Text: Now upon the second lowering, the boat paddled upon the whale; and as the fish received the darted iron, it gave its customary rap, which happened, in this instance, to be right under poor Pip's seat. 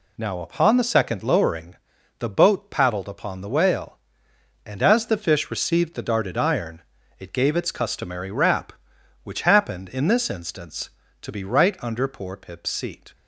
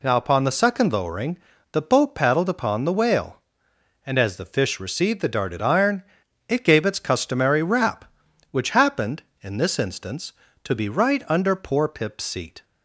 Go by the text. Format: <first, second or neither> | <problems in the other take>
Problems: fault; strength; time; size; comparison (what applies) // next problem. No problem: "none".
neither | none